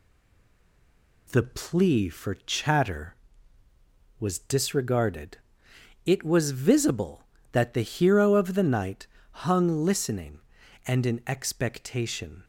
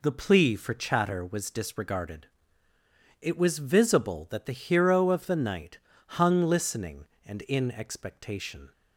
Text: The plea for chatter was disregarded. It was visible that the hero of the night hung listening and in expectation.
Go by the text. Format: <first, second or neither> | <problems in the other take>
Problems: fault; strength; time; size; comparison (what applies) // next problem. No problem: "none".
second | stays silent before the first word; noticeable; until 1.2 s; 1.2 s long // pauses between "night" and "hung"; at 9.0 s; 0.38 s long; also in the second